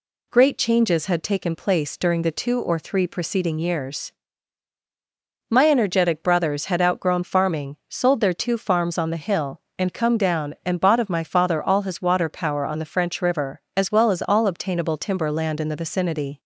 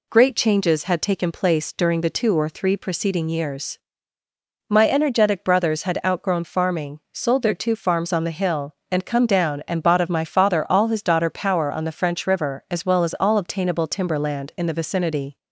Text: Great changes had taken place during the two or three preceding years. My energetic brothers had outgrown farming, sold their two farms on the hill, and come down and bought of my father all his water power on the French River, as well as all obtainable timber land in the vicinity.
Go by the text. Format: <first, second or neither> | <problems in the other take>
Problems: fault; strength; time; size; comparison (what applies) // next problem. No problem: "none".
first | says "daughter" for "water"; at 11.0 s